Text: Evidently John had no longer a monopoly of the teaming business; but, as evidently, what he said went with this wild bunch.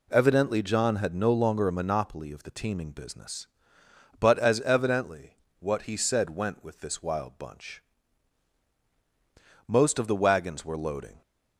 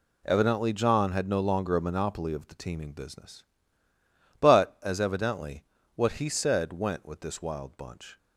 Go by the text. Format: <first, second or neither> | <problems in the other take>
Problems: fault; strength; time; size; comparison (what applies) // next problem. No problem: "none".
second | goes on to say "Most of the wagons were loading"; from 9.6 s on; 1.5 s long